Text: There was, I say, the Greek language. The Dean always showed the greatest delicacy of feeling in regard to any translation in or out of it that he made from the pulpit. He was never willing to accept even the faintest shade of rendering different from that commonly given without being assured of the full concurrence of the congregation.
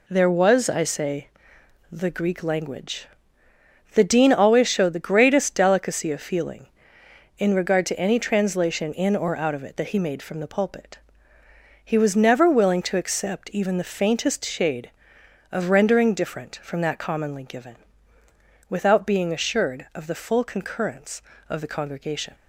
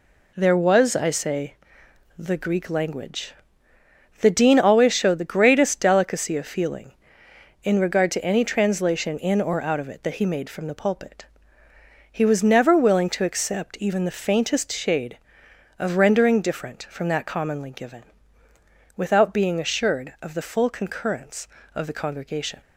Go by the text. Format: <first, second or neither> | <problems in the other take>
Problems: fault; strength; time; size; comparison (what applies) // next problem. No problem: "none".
neither | pauses between "given" and "without"; noticeable; the same in both